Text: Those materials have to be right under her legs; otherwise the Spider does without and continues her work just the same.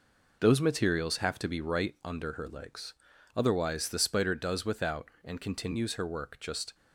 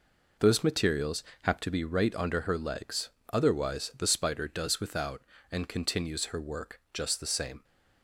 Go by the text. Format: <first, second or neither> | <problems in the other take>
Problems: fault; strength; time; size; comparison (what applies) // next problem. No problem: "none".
second | stops before "the same"; at 6.7 s